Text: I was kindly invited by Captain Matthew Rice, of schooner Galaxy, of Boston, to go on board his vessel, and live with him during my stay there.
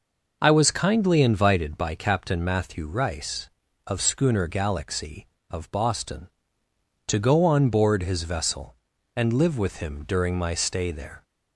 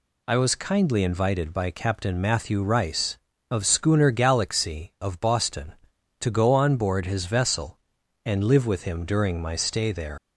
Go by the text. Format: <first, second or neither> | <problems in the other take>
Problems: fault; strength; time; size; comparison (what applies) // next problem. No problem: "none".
first | leaves "there" unfinished; at 10.1 s; 115 ms